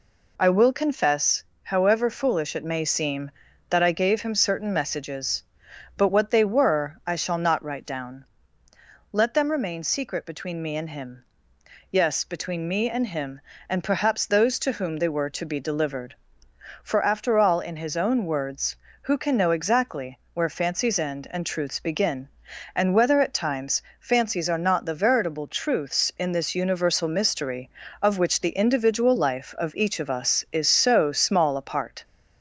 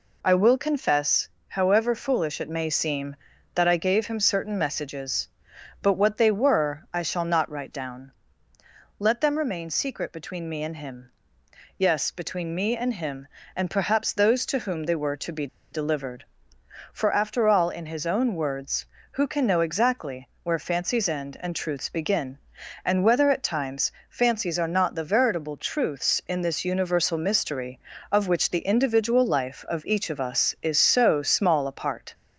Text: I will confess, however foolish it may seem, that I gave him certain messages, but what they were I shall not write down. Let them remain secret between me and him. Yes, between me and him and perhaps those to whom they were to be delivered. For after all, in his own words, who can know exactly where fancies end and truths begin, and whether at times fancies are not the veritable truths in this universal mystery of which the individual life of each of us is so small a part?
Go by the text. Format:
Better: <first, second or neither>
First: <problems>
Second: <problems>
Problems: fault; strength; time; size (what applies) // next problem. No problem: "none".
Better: first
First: pauses between "exactly" and "where"; slight; at 20.1 s; 0.16 s long // pauses between "times" and "fancies"; slight; at 23.8 s; 0.18 s long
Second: pauses between "be" and "delivered"; slight; at 15.4 s; 0.25 s long // pauses between "exactly" and "where"; slight; at 20.2 s; 0.16 s long // pauses between "times" and "fancies"; slight; at 23.9 s; 0.18 s long